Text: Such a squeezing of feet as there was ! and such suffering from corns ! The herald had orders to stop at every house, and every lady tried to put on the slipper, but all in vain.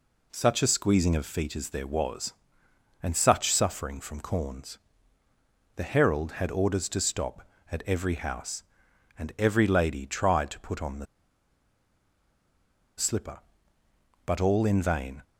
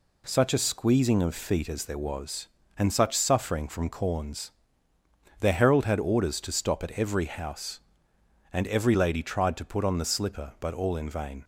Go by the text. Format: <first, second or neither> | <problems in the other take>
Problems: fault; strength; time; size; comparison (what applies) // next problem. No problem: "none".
second | pauses between "the" and "slipper"; strong; at 11.0 s; 1.9 s long